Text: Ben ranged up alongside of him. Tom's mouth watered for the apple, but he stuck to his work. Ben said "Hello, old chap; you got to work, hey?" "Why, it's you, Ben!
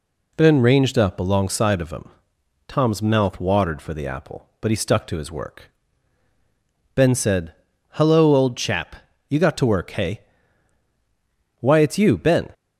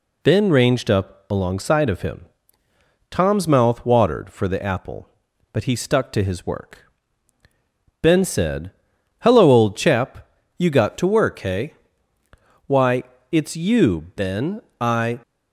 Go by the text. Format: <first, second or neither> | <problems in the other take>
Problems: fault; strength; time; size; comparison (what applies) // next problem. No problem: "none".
first | pauses between "said" and "Hello"; noticeable; at 8.7 s; 0.48 s long; also in the first // goes on to say "I"; slight; from 14.7 s on; 0.40 s long